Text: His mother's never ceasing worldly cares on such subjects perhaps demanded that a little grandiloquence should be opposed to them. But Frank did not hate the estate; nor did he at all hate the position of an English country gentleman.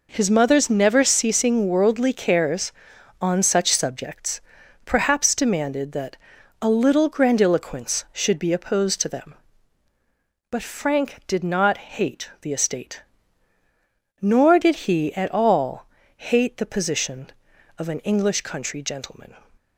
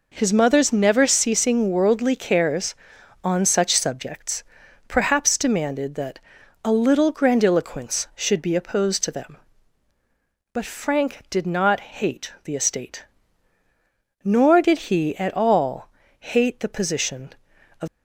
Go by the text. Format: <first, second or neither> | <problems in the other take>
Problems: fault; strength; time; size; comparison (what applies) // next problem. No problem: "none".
first | pauses between "subjects" and "perhaps"; at 4.4 s; 0.44 s long; also in the first // pauses between "that" and "a"; at 6.1 s; 0.44 s long; also in the first // pauses between "all" and "hate"; slight; at 15.8 s; 0.30 s long; slight in the first // stops before "an English country gentleman"; at 17.8 s